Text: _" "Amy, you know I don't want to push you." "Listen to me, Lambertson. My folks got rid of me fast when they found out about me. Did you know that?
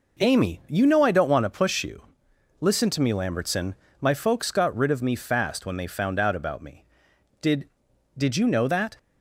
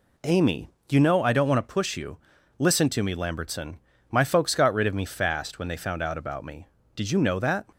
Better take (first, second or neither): second